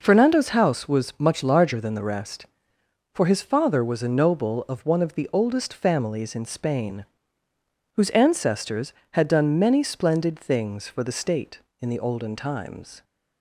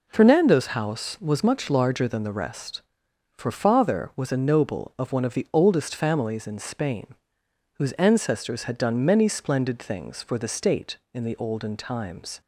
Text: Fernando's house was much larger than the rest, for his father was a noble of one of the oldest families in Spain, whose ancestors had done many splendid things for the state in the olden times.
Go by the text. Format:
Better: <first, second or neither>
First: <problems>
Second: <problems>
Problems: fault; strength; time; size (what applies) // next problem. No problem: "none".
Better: first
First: none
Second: skips "his"; at 3.5 s